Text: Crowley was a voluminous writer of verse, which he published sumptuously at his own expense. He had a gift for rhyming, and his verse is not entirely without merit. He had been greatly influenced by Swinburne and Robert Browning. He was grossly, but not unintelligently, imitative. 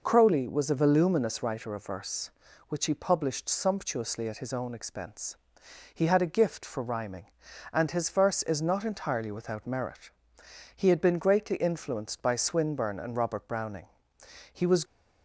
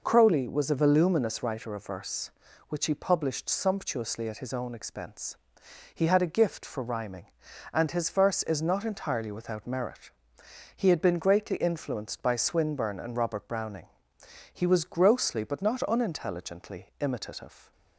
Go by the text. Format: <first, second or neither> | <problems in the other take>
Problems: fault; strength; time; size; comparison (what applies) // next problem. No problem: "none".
second | stops before "grossly but not unintelligently imitative"; at 14.8 s